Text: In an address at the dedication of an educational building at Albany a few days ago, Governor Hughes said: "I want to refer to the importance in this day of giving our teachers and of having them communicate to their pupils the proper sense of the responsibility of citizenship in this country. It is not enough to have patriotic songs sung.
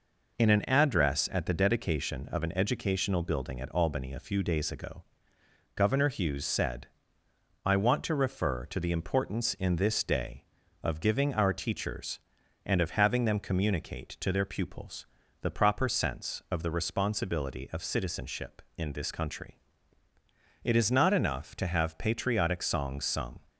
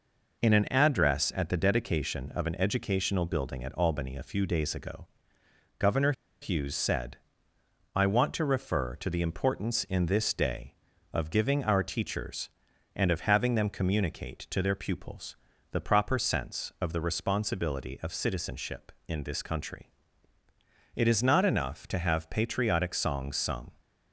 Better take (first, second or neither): first